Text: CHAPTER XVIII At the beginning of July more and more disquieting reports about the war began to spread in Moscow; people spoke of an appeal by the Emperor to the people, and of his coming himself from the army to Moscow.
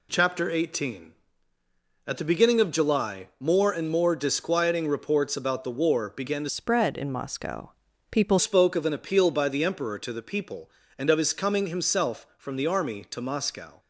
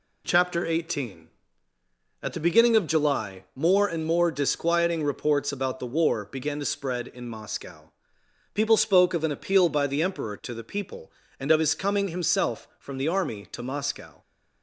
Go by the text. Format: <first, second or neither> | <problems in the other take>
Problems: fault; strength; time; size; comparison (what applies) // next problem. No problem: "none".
second | changes voice from "spread" to "people"; from 6.4 to 8.3 s; 1.9 s long